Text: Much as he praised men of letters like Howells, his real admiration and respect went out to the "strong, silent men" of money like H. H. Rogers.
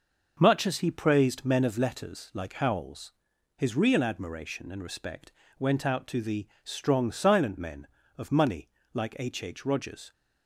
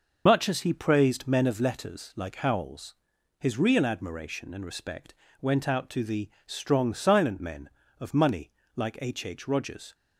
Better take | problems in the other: first | loses the start of "Much"; at 0.2 s; 60 ms // pauses between "respect" and "went"; slight; at 5.1 s; 0.26 s long; slight in the first // pauses between "the" and "strong"; slight; at 6.2 s; 0.16 s long; slight in the first // pauses between "money" and "like"; slight; at 8.5 s; 0.26 s long; slight in the first

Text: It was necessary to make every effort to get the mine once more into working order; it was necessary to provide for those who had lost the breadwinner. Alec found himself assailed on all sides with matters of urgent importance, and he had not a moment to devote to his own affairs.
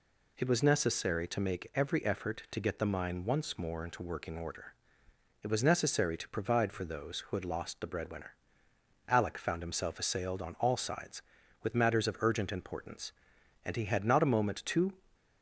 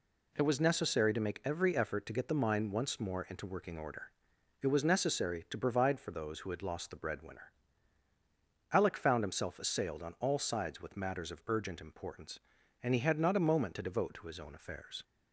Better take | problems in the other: second | stops before "devote to his own affairs"; at 15.1 s

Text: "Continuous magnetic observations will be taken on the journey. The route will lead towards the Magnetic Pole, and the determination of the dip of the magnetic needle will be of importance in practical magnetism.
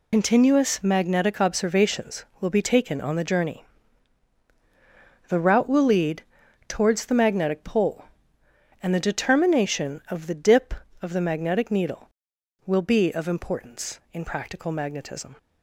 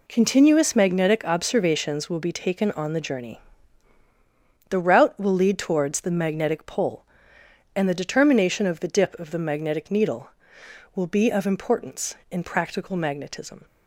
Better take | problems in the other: second | loses the start of "Continuous"; at 0.1 s; 75 ms // pauses between "lead" and "towards"; at 6.2 s; 0.44 s long

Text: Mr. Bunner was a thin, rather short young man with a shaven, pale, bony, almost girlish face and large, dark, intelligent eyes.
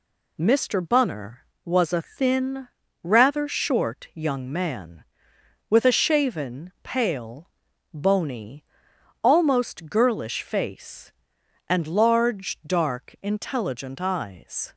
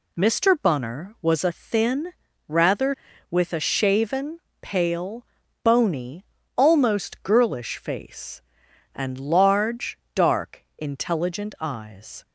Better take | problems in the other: first | skips "short young man"; at 3.1 s

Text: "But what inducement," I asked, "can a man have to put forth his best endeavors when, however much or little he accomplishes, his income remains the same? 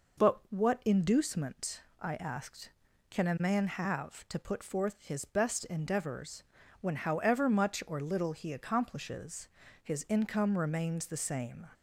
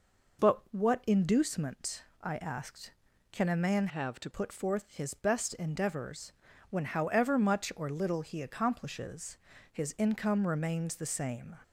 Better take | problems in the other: first | changes voice from "have" to "to"; from 3.8 to 4.2 s; 0.4 s long // pauses between "endeavors" and "when"; at 6.3 s; 0.40 s long; also in the first

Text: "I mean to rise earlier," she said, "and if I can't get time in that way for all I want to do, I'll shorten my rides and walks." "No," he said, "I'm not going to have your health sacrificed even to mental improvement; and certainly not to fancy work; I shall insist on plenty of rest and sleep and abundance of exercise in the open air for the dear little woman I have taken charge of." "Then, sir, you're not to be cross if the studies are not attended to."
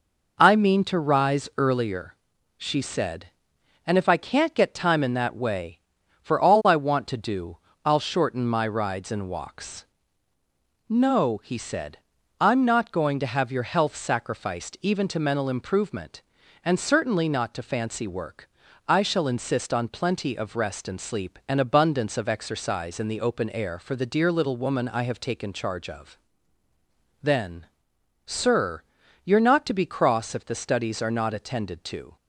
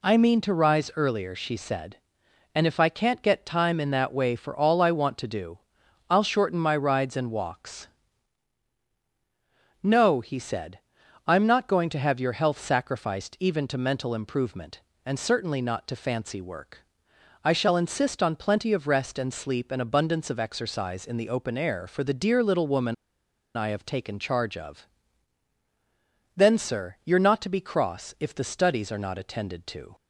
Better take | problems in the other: first | pauses between "woman" and "I"; noticeable; at 22.9 s; 0.60 s long

